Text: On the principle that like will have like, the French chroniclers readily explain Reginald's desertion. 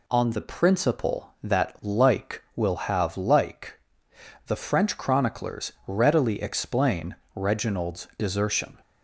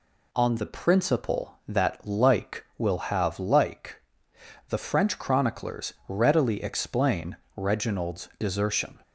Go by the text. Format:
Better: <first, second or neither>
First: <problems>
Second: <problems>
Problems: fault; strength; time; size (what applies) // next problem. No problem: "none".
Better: neither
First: pauses between "explain" and "Reginald's"; slight; at 7.1 s; 0.20 s long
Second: pauses between "explain" and "Reginald's"; slight; at 7.3 s; 0.20 s long